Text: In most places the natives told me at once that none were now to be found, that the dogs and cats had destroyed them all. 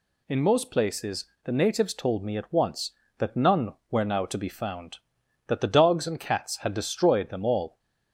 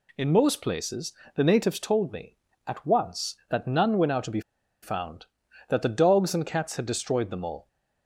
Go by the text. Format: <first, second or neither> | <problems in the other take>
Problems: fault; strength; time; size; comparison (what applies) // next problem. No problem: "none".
first | pauses between "places" and "the"; slight; at 1.1 s; 0.24 s long; slight in the first // pauses between "be" and "found"; at 4.3 s; 0.42 s long